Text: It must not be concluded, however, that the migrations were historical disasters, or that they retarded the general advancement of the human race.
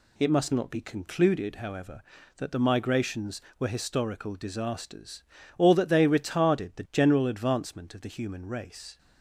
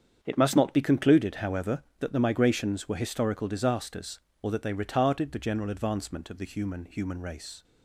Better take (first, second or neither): first